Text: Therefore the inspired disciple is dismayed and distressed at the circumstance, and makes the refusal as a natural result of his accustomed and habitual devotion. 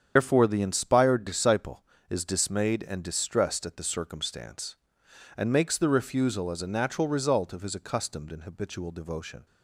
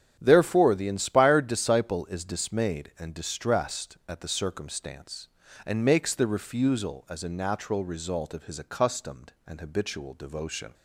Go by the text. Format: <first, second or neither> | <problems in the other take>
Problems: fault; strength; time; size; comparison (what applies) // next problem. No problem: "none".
second | loses the start of "Therefore"; at 0.1 s; 100 ms // starts louder than the rest; strong; until 1.1 s; 8 dB; strong in the second